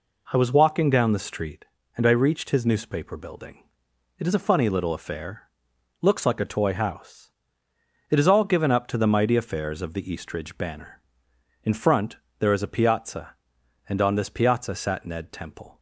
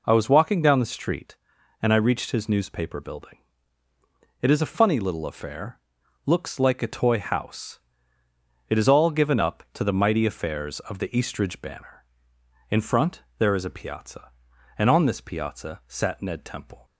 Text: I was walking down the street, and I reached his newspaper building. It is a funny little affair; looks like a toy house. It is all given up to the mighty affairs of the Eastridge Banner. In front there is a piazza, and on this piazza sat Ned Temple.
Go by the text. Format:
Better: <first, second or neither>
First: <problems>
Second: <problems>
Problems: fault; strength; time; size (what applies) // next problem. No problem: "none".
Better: neither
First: pauses between "front" and "there"; slight; at 12.1 s; 0.22 s long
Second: pauses between "front" and "there"; slight; at 13.2 s; 0.16 s long